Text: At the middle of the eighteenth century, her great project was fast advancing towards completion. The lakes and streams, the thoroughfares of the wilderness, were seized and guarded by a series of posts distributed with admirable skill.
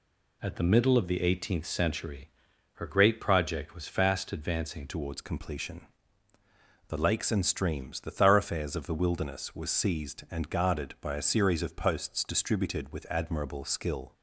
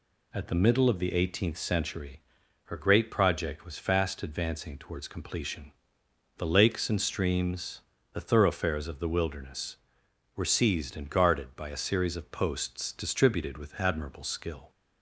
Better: second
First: changes voice at "towards"; from 4.8 s on; 9.3 s long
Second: none

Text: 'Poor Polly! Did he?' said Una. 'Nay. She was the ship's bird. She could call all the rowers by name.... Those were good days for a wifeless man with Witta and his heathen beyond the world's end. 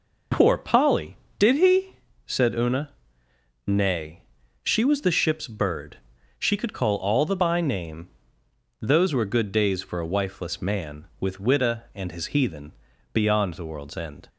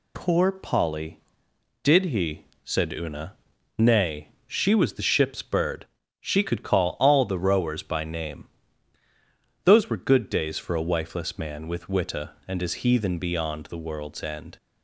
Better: second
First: skips "rowers"; at 7.3 s // pauses between "heathen" and "beyond"; at 12.7 s; 0.40 s long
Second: none

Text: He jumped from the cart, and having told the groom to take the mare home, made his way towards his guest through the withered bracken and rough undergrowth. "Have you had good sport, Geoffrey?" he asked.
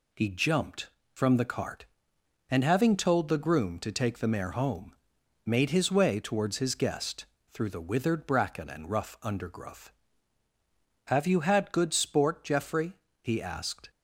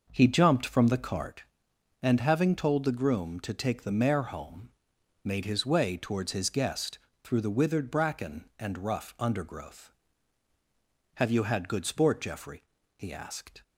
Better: first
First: pauses between "guest" and "through"; slight; at 7.2 s; 0.26 s long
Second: starts louder than the rest; noticeable; until 1.3 s; 6 dB // pauses between "guest" and "through"; slight; at 6.9 s; 0.24 s long

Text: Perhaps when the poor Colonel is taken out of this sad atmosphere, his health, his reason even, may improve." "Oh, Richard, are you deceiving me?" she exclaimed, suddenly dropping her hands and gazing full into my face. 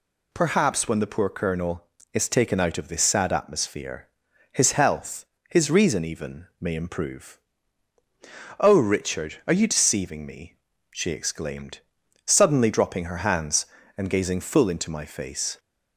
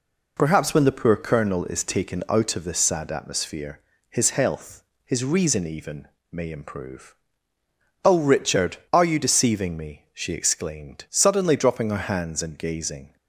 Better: first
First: none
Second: stops before "full into my face"; at 13.1 s

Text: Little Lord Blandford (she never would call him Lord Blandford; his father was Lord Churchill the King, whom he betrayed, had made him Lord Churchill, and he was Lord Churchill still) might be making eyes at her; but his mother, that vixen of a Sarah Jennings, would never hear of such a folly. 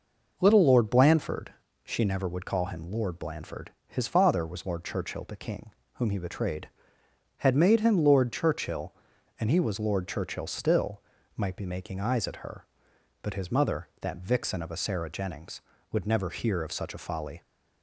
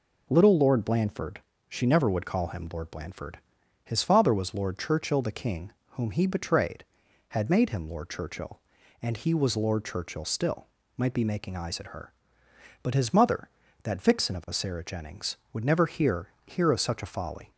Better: first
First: none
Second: says "hear" twice; at 16.4 s

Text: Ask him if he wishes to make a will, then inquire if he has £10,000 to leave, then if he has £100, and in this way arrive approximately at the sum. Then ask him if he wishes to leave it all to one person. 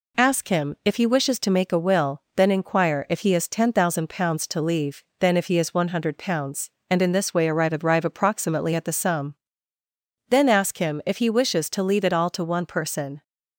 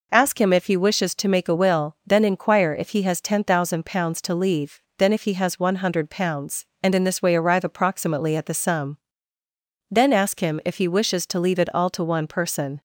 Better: second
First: says "arrive" twice; at 7.8 s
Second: none

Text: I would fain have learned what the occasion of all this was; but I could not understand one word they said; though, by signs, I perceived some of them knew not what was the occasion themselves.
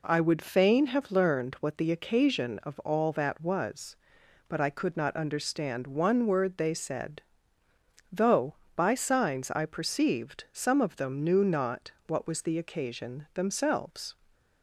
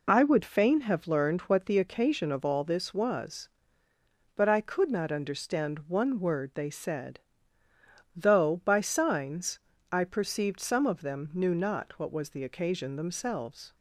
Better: second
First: says "that" for "this"; at 3.1 s // pauses between "not" and "what"; slight; at 11.9 s; 0.16 s long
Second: none

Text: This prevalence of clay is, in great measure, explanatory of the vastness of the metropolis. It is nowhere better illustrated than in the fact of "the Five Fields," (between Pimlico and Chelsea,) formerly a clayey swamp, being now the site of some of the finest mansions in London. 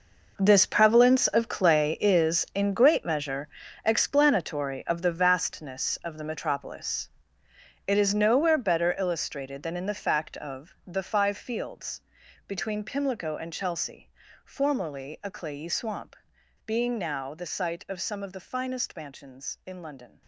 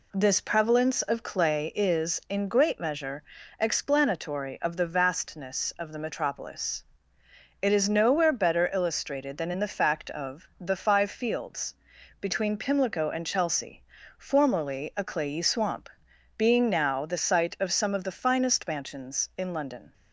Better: second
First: gets quieter; strong; throughout; 13 dB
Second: none

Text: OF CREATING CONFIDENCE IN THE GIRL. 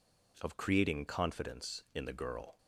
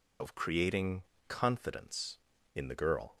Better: first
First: none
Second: loses the start of "OF"; at 0.2 s; 35 ms // pauses between "CREATING" and "CONFIDENCE"; slight; at 1.0 s; 0.23 s long

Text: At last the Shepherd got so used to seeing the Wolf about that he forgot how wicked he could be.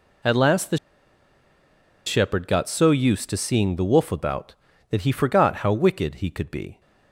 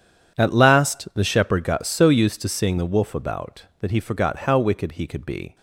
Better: second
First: pauses between "the" and "Shepherd"; strong; at 0.7 s; 1.2 s long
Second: none

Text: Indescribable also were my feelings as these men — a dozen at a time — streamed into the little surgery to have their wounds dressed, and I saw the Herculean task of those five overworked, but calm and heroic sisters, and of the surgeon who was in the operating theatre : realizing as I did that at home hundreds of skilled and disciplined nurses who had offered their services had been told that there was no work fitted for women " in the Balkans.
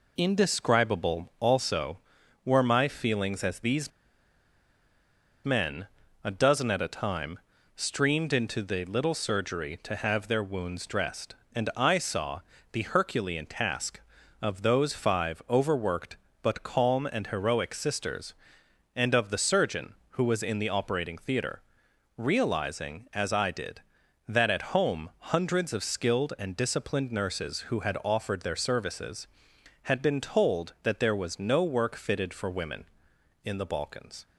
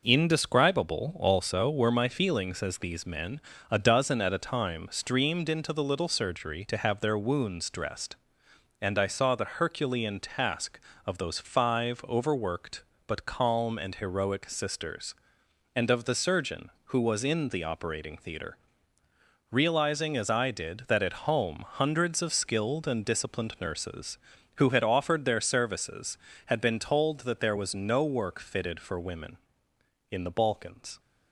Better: second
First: pauses between "these" and "men"; strong; at 3.9 s; 1.5 s long // pauses between "saw" and "the"; slight; at 12.3 s; 0.32 s long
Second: none

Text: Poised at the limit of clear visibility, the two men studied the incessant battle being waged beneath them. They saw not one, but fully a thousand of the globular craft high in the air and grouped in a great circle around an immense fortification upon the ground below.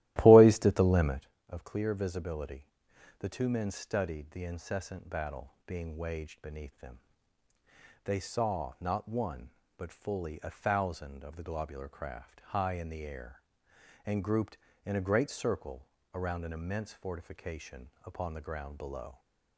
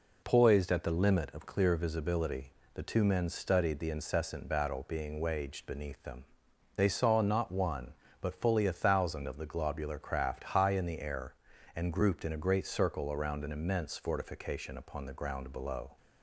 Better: second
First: starts louder than the rest; strong; until 1.2 s; 15 dB // pauses between "circle" and "around"; slight; at 15.8 s; 0.30 s long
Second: none

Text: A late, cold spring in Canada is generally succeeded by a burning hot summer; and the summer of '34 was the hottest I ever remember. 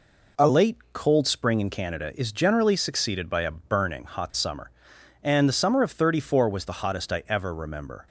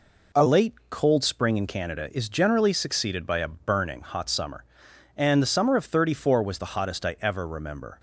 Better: neither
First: none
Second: none

